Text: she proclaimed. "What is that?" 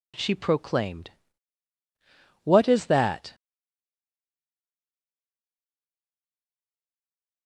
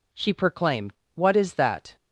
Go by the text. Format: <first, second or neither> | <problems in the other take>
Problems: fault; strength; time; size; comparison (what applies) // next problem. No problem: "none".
second | stays silent after the last word; strong; from 3.3 s on; 4.1 s long